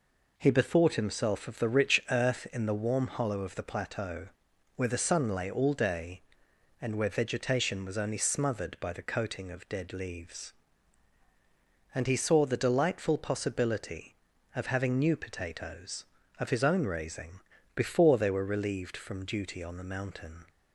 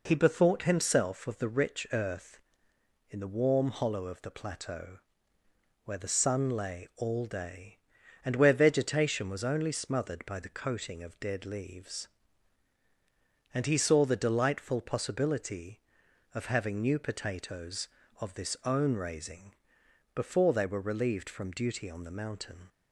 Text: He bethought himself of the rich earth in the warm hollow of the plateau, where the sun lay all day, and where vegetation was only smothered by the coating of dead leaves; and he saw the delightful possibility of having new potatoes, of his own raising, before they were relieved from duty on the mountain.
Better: first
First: none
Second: says "this" for "his"; at 18.3 s

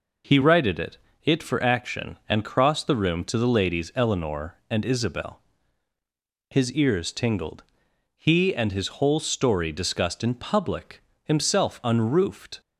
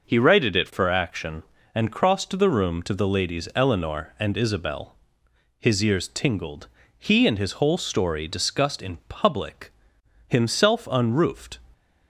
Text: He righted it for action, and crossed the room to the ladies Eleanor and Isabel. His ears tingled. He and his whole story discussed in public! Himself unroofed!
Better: second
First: says "it" twice; at 1.2 s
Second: none

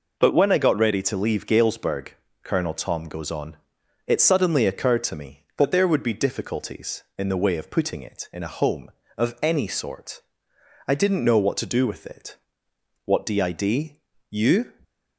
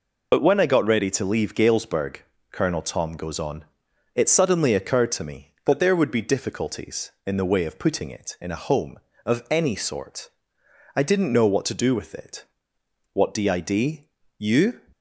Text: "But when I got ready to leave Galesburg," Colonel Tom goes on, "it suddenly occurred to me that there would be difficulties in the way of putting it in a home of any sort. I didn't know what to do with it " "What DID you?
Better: first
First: pauses between "DID" and "you"; slight; at 13.9 s; 0.32 s long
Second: loses the start of "But"; at 0.3 s; 50 ms // pauses between "DID" and "you"; slight; at 14.0 s; 0.32 s long

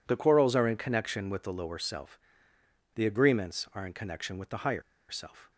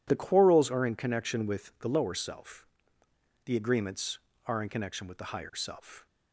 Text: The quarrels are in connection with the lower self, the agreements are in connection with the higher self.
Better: second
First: pauses between "higher" and "self"; slight; at 4.8 s; 0.28 s long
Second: none

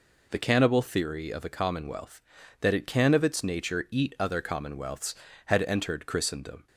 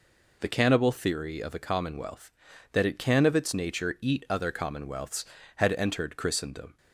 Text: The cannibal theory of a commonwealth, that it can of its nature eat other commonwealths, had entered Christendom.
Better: neither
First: none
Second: none

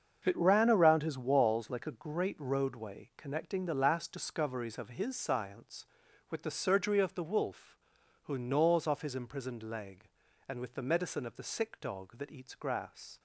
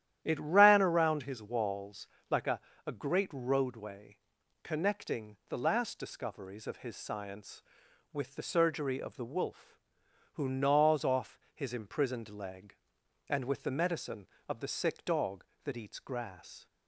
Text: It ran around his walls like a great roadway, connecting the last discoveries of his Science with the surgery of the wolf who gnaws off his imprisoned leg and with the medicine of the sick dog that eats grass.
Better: first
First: starts louder than the rest; until 1.2 s; 6.5 dB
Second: starts louder than the rest; strong; until 1.2 s; 11.5 dB // pauses between "walls" and "like"; slight; at 2.0 s; 0.24 s long // says "a" twice; at 2.8 s // pauses between "off" and "his"; slight; at 11.3 s; 0.16 s long

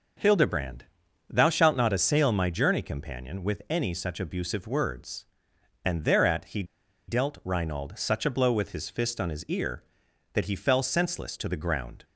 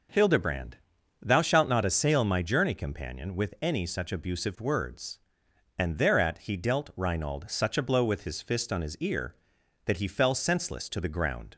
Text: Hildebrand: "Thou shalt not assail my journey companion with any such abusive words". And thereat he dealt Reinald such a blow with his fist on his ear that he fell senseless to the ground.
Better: second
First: pauses between "he" and "dealt"; at 6.6 s; 0.44 s long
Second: none

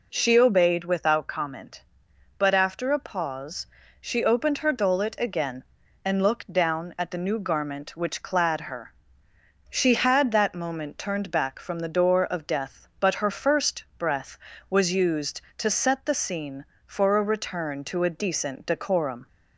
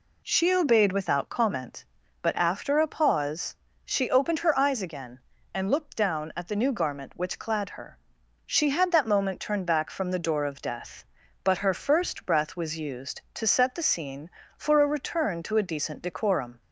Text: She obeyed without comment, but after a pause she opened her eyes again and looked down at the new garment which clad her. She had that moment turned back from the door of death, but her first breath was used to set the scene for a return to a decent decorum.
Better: second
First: pauses between "pause" and "she"; slight; at 3.6 s; 0.36 s long // says "dolet" for "eyes"; at 4.7 s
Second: pauses between "pause" and "she"; slight; at 3.5 s; 0.28 s long

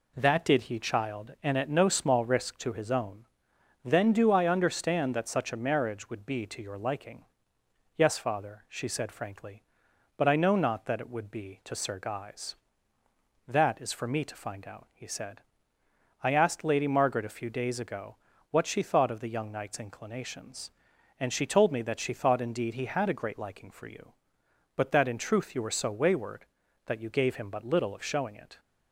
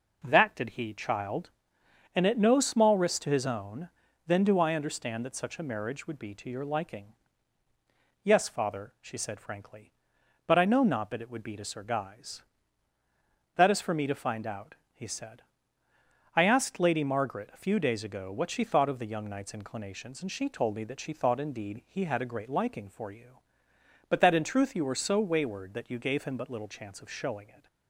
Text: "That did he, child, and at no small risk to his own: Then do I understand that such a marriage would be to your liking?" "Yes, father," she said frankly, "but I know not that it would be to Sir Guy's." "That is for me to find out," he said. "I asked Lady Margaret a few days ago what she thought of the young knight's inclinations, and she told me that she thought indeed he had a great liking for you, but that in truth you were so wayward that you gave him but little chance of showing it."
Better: second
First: pauses between "ago" and "what"; slight; at 18.1 s; 0.36 s long // skips "chance"; at 27.9 s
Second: none

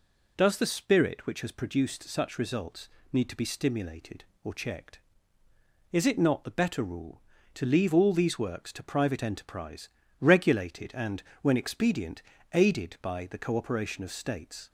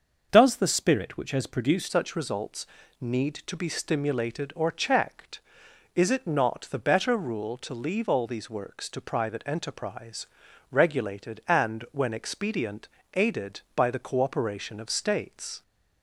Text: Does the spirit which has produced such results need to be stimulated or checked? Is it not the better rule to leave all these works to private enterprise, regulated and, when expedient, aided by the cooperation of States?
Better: first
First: pauses between "results" and "need"; slight; at 2.8 s; 0.24 s long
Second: starts louder than the rest; until 1.3 s; 6.5 dB // changes voice at "such"; from 1.8 s on; 13.8 s long // pauses between "results" and "need"; slight; at 2.6 s; 0.34 s long

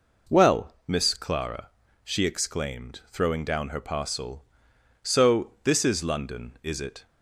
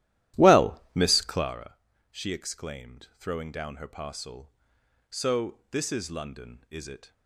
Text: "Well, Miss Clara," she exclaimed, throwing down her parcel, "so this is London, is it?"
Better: first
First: none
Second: starts louder than the rest; strong; until 1.6 s; 14 dB

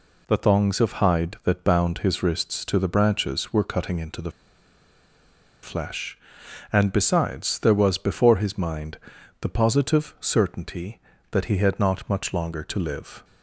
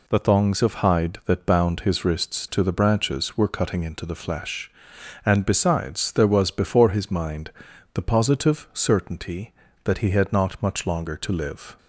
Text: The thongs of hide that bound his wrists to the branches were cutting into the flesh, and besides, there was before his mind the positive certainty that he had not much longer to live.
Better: second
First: pauses between "the" and "flesh"; strong; at 4.3 s; 1.3 s long // pauses between "mind" and "the"; at 8.9 s; 0.42 s long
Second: pauses between "mind" and "the"; at 7.5 s; 0.42 s long

